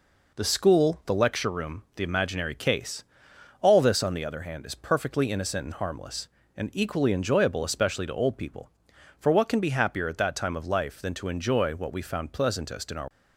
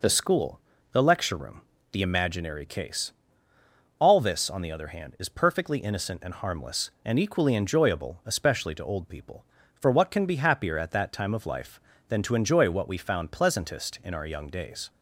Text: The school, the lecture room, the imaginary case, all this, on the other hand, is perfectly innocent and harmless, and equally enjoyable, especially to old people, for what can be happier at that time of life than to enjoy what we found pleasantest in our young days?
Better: second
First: stops before "young days"; at 13.0 s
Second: none

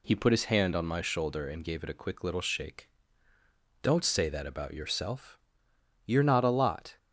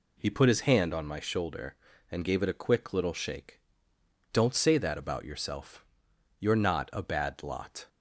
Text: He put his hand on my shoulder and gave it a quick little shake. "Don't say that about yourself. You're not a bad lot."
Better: second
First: skips "bad"; at 6.5 s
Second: none

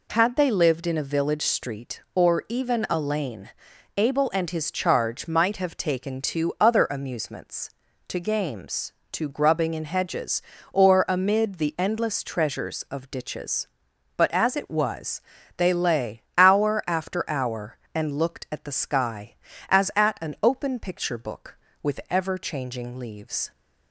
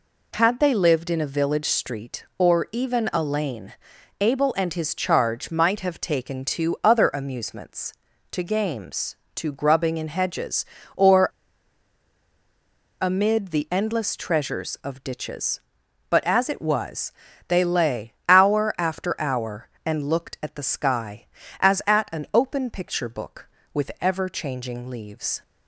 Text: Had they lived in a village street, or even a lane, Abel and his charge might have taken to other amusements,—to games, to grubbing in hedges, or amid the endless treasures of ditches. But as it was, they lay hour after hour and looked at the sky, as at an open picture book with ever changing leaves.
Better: first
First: none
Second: pauses between "or" and "amid"; strong; at 11.2 s; 1.7 s long

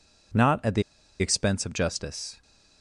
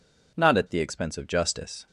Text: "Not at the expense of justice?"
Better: second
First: pauses between "the" and "expense"; at 0.8 s; 0.37 s long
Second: none

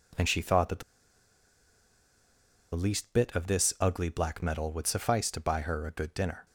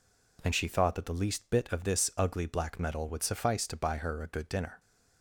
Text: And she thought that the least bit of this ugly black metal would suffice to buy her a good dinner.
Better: second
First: pauses between "the" and "least"; strong; at 0.8 s; 1.9 s long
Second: none

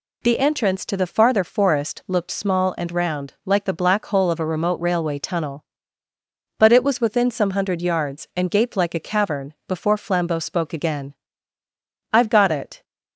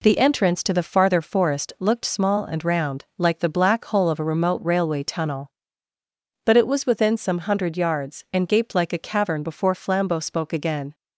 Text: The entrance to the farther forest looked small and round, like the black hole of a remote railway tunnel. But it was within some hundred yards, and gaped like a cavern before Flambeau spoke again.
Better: second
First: goes on to say "I've got it"; noticeable; from 12.1 s on; 0.70 s long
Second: none

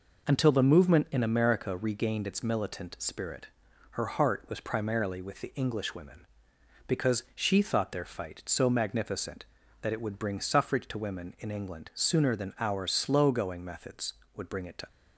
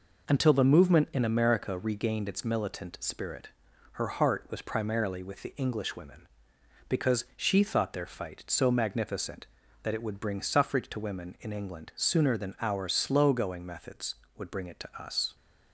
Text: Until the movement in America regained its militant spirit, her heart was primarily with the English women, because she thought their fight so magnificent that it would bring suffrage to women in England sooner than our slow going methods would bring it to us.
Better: second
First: stops before "us"; at 14.8 s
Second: none

